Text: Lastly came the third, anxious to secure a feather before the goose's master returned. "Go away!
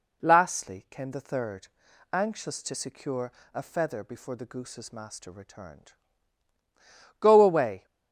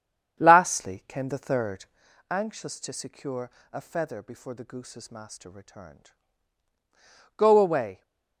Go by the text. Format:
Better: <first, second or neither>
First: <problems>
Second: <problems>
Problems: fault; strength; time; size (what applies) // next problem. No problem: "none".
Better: first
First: pauses between "secure" and "a"; slight; at 3.3 s; 0.22 s long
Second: starts louder than the rest; strong; until 2.1 s; 8 dB // pauses between "secure" and "a"; slight; at 3.4 s; 0.22 s long